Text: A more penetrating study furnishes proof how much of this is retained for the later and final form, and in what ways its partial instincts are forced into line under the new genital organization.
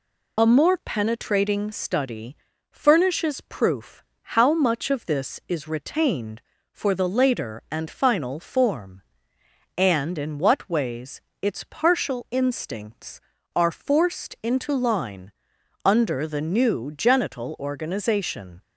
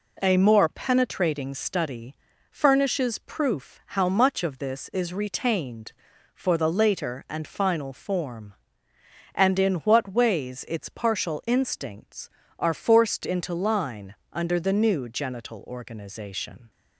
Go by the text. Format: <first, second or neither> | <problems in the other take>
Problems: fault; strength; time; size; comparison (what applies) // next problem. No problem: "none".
second | loses the start of "A"; at 0.3 s; 40 ms // pauses between "study" and "furnishes"; slight; at 2.3 s; 0.34 s long; slight in the second // pauses between "proof" and "how"; slight; at 4.0 s; 0.18 s long // pauses between "ways" and "its"; slight; at 11.1 s; 0.22 s long // pauses between "line" and "under"; noticeable; at 15.3 s; 0.52 s long; slight in the second